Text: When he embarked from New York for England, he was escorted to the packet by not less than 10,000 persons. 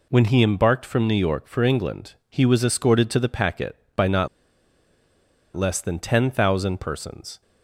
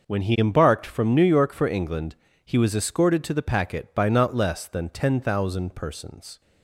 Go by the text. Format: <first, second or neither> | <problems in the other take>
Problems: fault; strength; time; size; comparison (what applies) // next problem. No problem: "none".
second | pauses between "not" and "less"; strong; at 4.2 s; 1.2 s long